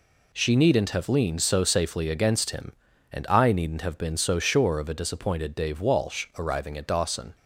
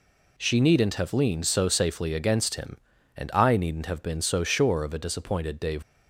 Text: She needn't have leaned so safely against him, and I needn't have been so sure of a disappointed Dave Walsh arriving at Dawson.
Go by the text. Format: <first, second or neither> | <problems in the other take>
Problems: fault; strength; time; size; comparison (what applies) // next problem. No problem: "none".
first | stops before "Walsh arriving at Dawson"; at 5.8 s